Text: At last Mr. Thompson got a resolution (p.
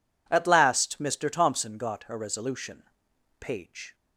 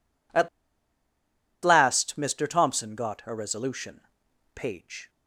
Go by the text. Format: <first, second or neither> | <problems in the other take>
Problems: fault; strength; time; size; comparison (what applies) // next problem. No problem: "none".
first | pauses between "At" and "last"; at 0.4 s; 1.1 s long